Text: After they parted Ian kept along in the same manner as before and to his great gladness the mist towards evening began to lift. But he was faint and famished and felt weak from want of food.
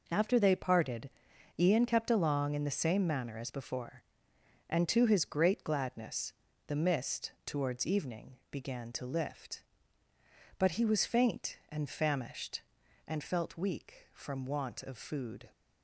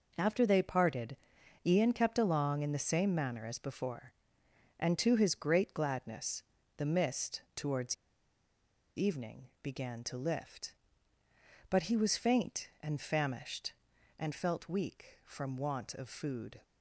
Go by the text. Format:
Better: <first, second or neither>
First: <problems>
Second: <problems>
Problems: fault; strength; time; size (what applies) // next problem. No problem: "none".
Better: first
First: pauses between "parted" and "Ian"; noticeable; at 1.0 s; 0.50 s long // pauses between "gladness" and "the"; slight; at 6.3 s; 0.34 s long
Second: pauses between "parted" and "Ian"; noticeable; at 1.1 s; 0.50 s long // pauses between "gladness" and "the"; slight; at 6.4 s; 0.34 s long // pauses between "towards" and "evening"; at 7.9 s; 1.0 s long